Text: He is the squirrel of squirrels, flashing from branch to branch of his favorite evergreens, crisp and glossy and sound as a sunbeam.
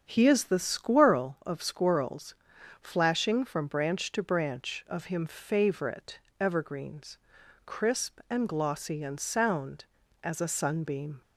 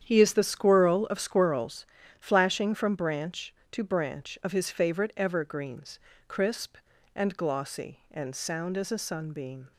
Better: second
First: starts louder than the rest; strong; until 1.1 s; 8 dB // says "him" for "his"; at 5.0 s // pauses between "favorite" and "evergreens"; slight; at 6.1 s; 0.20 s long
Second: starts louder than the rest; strong; until 1.0 s; 9 dB

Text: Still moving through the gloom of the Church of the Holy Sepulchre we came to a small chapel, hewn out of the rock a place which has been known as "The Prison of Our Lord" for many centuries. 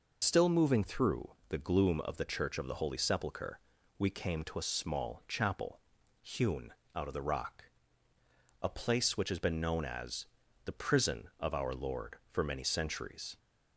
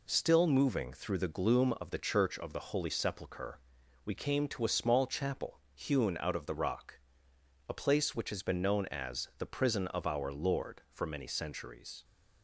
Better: second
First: loses the start of "Still"; at 0.2 s; 100 ms // pauses between "through" and "the"; slight; at 1.3 s; 0.18 s long // pauses between "Sepulchre" and "we"; at 3.5 s; 0.38 s long // pauses between "hewn" and "out"; slight; at 6.7 s; 0.24 s long // pauses between "rock" and "a"; noticeable; at 7.6 s; 0.96 s long // pauses between "as" and "The"; at 10.2 s; 0.38 s long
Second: pauses between "Sepulchre" and "we"; at 3.5 s; 0.44 s long // pauses between "rock" and "a"; noticeable; at 6.9 s; 0.68 s long

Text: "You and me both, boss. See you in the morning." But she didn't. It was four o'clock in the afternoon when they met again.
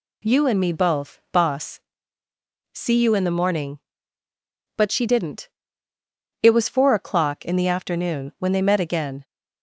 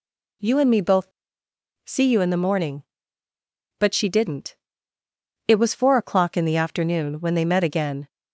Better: first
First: none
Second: skips "boss"; at 1.4 s

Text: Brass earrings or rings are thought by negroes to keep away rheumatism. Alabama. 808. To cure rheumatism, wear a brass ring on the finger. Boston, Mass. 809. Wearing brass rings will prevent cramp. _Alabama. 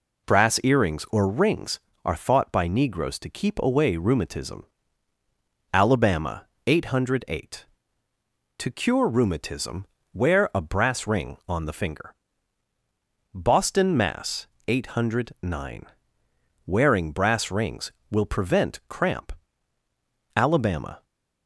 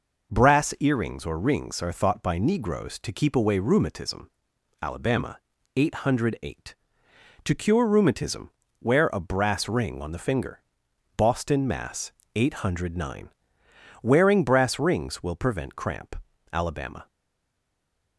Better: first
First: none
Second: stays silent after the last word; from 17.0 s on; 1.1 s long

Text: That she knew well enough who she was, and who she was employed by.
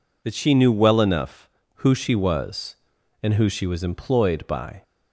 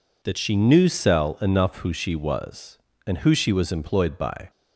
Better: first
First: none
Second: says "cell" for "well"; at 0.8 s

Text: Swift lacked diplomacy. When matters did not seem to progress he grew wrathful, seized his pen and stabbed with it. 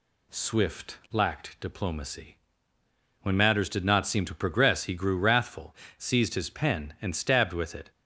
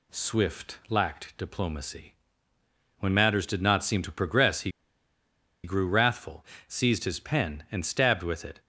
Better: first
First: none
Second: pauses between "he" and "grew"; noticeable; at 4.7 s; 0.93 s long

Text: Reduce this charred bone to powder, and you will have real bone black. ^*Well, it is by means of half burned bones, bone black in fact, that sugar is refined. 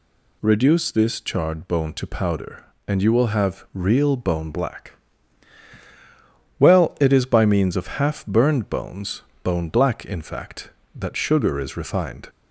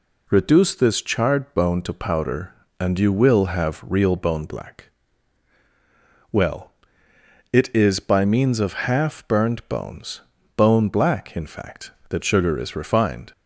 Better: neither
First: none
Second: none

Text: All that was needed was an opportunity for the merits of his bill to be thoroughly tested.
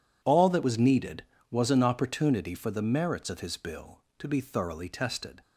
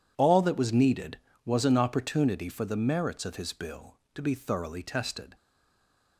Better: first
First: none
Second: stays silent after the last word; slight; from 5.3 s on; 0.8 s long

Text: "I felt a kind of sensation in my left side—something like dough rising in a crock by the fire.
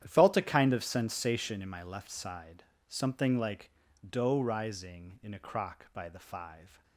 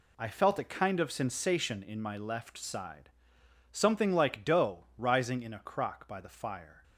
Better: second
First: starts louder than the rest; strong; until 1.0 s; 10.5 dB // pauses between "like" and "dough"; slight; at 3.7 s; 0.36 s long // says "five" for "fire"; at 6.1 s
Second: none

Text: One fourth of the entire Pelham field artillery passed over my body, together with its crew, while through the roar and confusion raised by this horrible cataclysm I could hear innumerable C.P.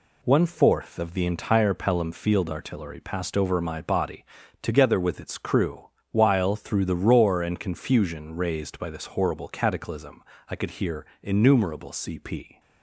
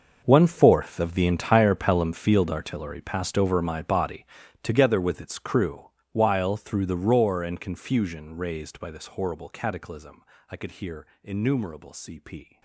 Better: first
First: pauses between "cataclysm" and "I"; slight; at 10.2 s; 0.26 s long // pauses between "hear" and "innumerable"; slight; at 11.0 s; 0.18 s long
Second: gets quieter; strong; throughout; 16 dB // pauses between "cataclysm" and "I"; slight; at 10.2 s; 0.26 s long // pauses between "hear" and "innumerable"; slight; at 11.0 s; 0.18 s long

